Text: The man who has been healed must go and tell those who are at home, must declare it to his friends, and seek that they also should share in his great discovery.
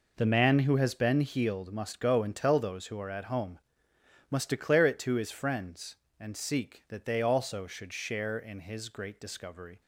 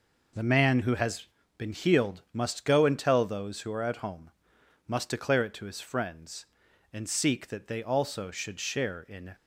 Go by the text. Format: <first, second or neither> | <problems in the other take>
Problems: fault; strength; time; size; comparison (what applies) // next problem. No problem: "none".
first | pauses between "has" and "been"; slight; at 1.2 s; 0.32 s long // stops before "his great discovery"; at 9.3 s